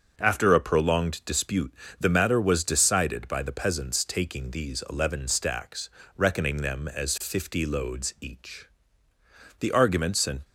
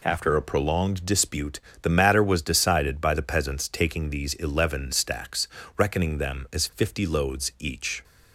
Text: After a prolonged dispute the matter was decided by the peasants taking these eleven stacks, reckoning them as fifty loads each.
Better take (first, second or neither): second